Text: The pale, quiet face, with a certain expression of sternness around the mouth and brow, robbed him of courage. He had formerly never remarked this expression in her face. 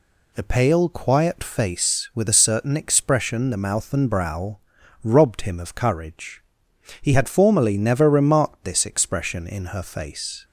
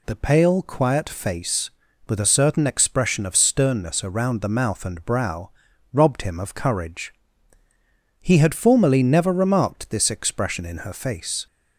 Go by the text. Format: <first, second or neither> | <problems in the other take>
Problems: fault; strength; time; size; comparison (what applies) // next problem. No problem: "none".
second | skips "of sternness around"; at 3.5 s